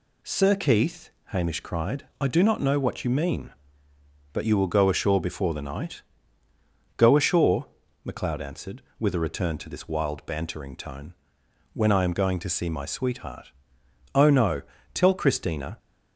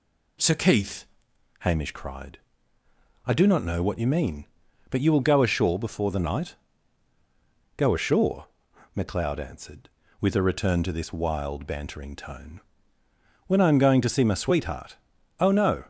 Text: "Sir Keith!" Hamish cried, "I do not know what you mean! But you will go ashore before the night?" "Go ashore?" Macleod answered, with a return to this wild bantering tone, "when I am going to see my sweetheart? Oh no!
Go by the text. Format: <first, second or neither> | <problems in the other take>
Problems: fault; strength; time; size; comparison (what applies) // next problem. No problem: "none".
second | goes on to say "Tell Christina"; noticeable; from 14.9 s on; 0.84 s long